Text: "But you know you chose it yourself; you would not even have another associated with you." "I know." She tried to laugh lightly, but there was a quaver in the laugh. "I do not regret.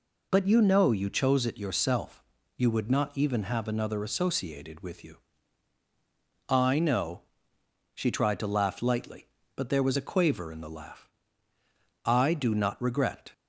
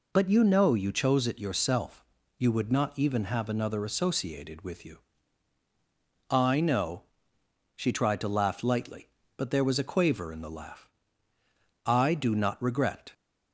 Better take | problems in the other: neither | none

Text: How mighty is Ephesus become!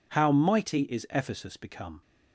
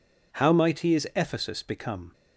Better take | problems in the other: neither | none

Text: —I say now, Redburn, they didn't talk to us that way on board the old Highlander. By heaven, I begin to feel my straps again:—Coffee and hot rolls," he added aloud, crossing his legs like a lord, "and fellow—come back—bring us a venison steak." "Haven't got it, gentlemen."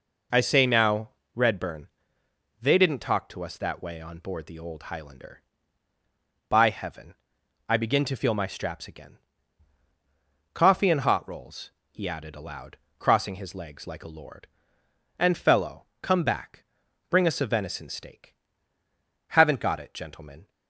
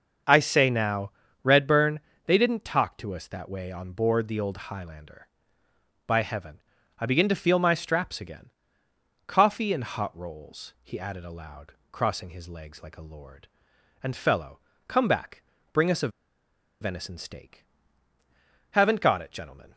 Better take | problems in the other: first | starts louder than the rest; until 1.5 s; 6.5 dB // pauses between "a" and "venison"; noticeable; at 16.0 s; 0.72 s long

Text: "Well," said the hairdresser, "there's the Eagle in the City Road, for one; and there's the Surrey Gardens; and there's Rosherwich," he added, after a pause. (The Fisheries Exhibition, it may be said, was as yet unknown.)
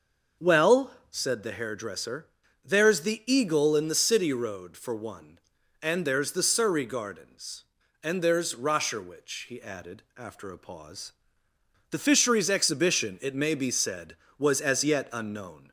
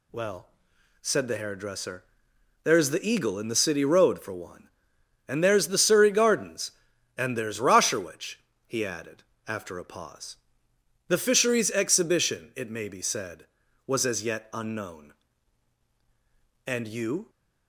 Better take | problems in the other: first | goes on to say "And you"; noticeable; from 16.6 s on; 0.64 s long

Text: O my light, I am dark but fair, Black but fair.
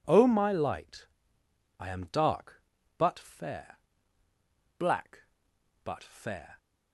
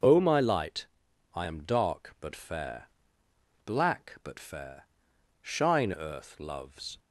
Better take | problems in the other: first | goes on to say "Shine Earth loves"; from 5.4 s on; 1.5 s long

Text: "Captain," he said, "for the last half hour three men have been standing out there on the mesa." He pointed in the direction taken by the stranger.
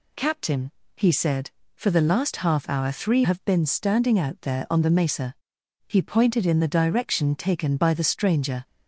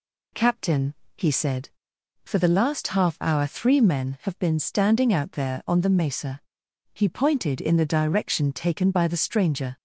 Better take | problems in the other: second | skips "men"; at 3.2 s

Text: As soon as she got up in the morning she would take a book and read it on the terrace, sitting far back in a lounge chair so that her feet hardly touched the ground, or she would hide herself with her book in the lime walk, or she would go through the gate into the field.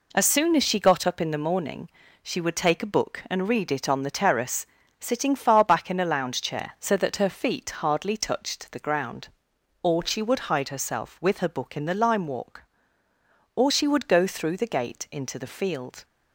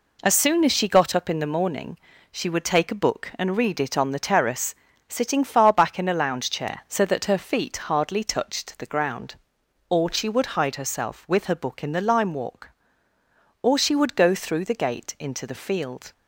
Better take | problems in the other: neither | pauses between "morning" and "she"; slight; the same in both

